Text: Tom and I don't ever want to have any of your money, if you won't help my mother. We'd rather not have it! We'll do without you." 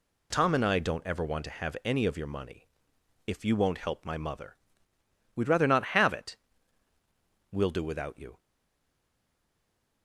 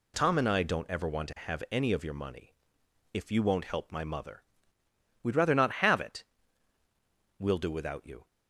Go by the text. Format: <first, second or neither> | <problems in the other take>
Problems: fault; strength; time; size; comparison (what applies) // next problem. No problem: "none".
second | stays silent after the last word; noticeable; from 8.3 s on; 1.7 s long